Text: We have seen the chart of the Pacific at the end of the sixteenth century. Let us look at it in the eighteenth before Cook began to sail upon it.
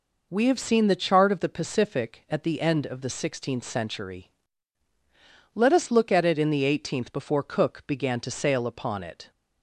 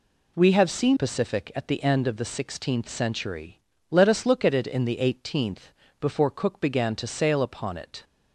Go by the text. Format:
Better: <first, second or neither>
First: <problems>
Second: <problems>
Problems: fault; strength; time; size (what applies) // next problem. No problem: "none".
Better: first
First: none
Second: skips "the chart of the"; at 0.9 s // pauses between "eighteenth" and "before"; slight; at 5.7 s; 0.28 s long